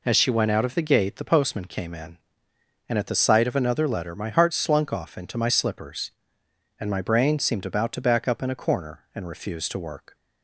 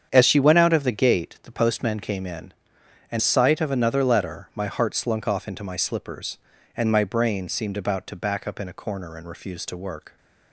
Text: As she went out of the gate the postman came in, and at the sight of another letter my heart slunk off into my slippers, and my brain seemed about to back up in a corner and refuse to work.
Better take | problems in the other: first | starts louder than the rest; strong; until 1.1 s; 8 dB // skips "at the"; at 3.2 s

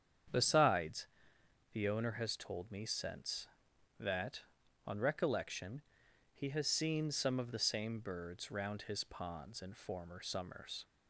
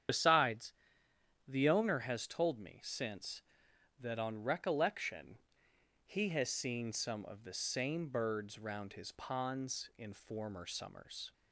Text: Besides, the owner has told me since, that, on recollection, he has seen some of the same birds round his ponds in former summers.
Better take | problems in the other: first | loses the start of "Besides"; at 0.0 s; 50 ms // starts louder than the rest; strong; until 1.8 s; 9 dB; strong in the first

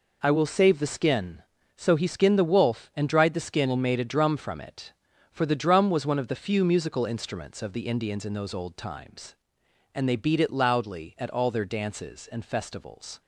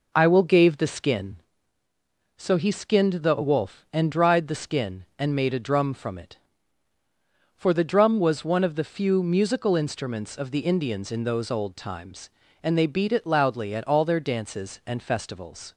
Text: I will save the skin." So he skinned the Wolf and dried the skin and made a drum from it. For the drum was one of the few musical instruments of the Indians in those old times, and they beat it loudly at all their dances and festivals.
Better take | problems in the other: first | says "gave" for "save"; at 0.4 s

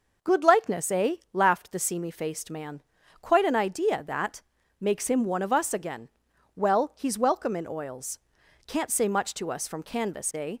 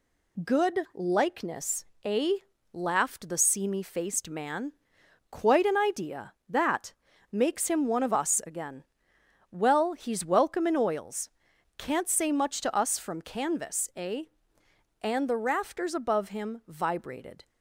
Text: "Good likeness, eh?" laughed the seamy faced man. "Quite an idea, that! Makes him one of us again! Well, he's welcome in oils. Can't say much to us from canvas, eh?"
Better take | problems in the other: first | goes on to say "And the rafters above him vibrated"; strong; from 14.9 s on; 2.4 s long

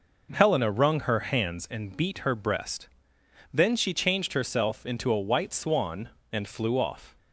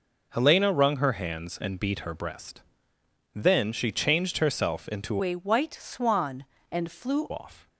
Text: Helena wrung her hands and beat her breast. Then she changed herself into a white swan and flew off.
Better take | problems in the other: first | changes voice from "a" to "flew"; from 5.2 to 7.3 s; 2.1 s long

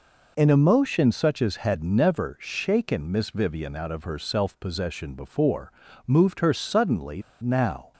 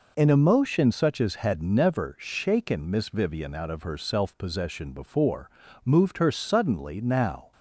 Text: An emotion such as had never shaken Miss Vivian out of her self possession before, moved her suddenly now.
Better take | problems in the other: second | pauses between "suddenly" and "now"; slight; at 7.2 s; 0.19 s long

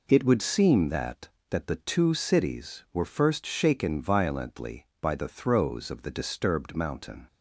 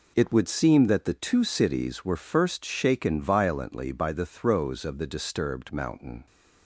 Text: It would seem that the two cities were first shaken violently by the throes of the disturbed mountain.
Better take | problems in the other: second | says "that" twice; at 1.4 s

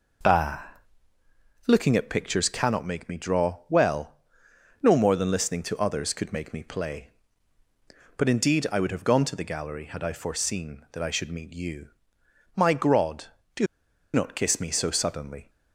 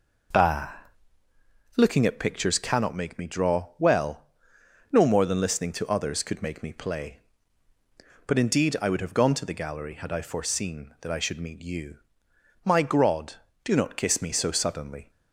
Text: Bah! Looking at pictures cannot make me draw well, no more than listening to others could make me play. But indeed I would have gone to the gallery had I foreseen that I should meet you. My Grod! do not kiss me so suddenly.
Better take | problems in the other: second | pauses between "do" and "not"; noticeable; at 13.6 s; 0.48 s long

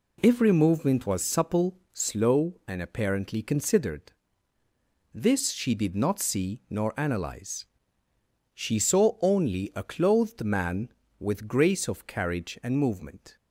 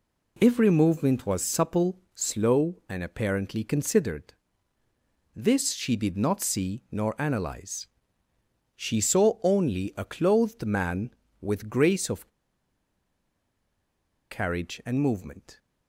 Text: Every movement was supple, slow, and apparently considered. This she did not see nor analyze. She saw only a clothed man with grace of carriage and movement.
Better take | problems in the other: first | pauses between "of" and "carriage"; strong; at 12.2 s; 2.0 s long

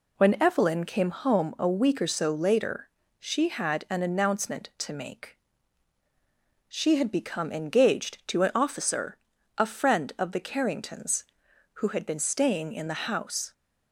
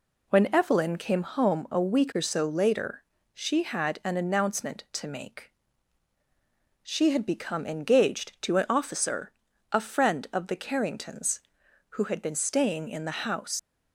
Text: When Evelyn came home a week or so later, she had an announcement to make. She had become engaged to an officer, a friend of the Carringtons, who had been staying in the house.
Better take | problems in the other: first | leaves "house" unfinished; at 13.5 s; 105 ms

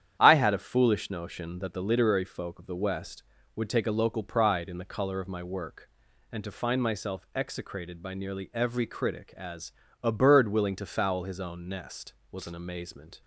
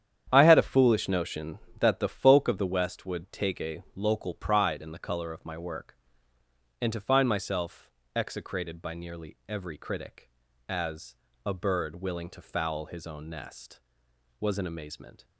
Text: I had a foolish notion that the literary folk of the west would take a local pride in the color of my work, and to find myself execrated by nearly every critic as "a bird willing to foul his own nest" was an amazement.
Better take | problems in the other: first | starts louder than the rest; strong; until 1.3 s; 9.5 dB; strong in the first // skips "literary"; at 2.0 s // pauses between "myself" and "execrated"; slight; at 7.8 s; 0.26 s long // pauses between "as" and "a"; slight; at 11.1 s; 0.32 s long; slight in the first

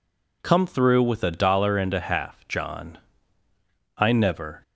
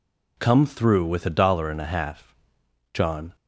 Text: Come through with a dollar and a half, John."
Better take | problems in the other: second | goes on to say "I never"; noticeable; from 3.9 s on; 0.64 s long

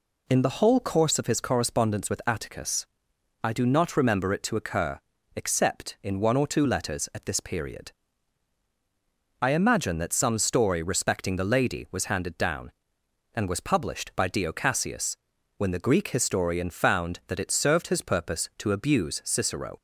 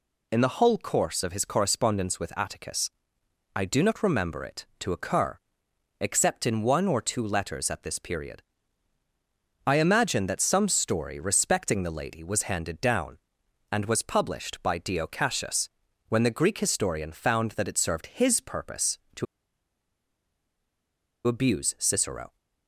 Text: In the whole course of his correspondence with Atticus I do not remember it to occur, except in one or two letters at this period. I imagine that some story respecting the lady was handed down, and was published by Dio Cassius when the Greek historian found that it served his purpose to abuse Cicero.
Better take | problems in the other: first | pauses between "Atticus" and "I"; noticeable; at 2.8 s; 0.64 s long; noticeable in the first // pauses between "Cassius" and "when"; at 15.6 s; 0.40 s long; also in the first // pauses between "to" and "abuse"; strong; at 19.2 s; 2.0 s long

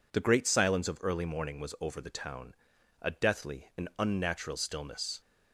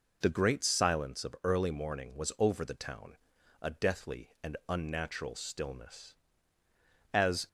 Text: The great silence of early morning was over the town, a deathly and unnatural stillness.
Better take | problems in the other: first | goes on to say "As"; slight; from 7.1 s on; 0.36 s long

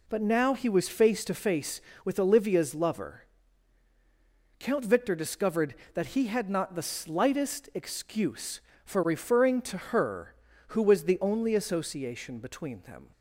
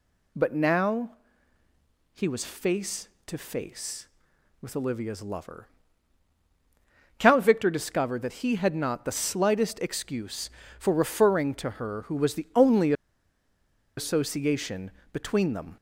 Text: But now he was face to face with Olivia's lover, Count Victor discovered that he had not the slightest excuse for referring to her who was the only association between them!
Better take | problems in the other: first | pauses between "now" and "he"; at 1.1 s; 1.0 s long // pauses between "only" and "association"; at 12.9 s; 1.0 s long // pauses between "association" and "between"; slight; at 14.9 s; 0.20 s long

